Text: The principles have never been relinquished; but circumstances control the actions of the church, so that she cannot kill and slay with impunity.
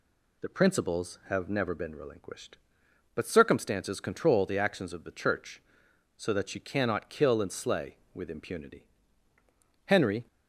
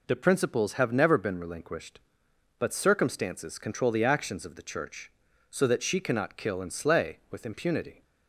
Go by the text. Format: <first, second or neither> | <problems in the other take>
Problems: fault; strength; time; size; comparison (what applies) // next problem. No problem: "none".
second | goes on to say "Henry"; slight; from 9.8 s on; 0.40 s long